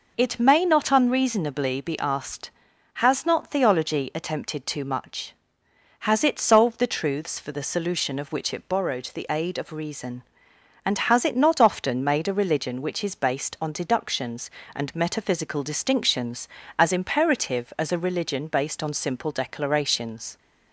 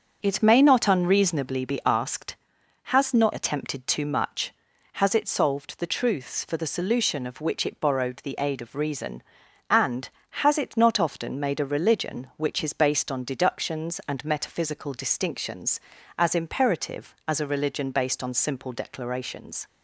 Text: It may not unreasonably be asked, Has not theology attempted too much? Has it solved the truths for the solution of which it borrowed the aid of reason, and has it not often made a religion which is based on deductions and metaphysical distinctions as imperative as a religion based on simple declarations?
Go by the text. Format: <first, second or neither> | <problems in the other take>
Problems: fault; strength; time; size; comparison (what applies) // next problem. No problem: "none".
first | starts louder than the rest; until 1.2 s; 7 dB // skips "theology"; at 3.3 s